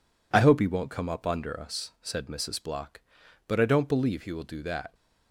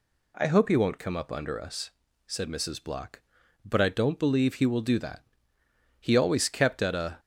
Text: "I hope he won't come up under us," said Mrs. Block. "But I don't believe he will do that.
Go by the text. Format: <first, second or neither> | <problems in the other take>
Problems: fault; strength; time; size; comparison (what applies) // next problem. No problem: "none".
first | goes on to say "He always kept at a"; noticeable; from 5.9 s on; 1.2 s long